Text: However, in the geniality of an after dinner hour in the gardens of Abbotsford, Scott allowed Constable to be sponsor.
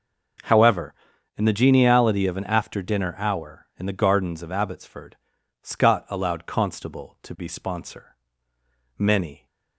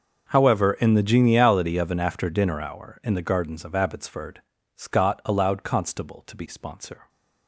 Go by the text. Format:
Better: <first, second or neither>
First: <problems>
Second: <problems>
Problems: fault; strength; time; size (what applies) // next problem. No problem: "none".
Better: second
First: goes on to say "Many"; slight; from 8.9 s on; 0.48 s long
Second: none